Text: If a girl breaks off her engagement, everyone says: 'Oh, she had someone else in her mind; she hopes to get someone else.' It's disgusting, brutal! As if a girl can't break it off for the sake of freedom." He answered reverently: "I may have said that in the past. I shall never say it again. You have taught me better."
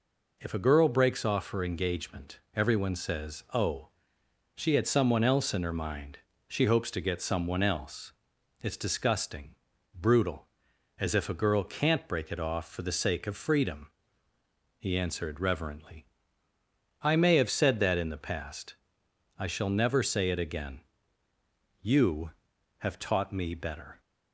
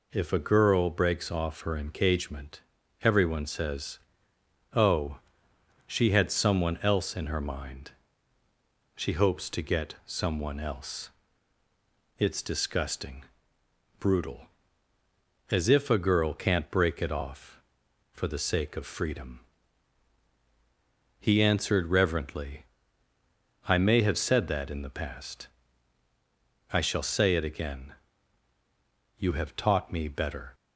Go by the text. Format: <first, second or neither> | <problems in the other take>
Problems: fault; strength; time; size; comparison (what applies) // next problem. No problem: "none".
first | skips "never"; at 27.0 s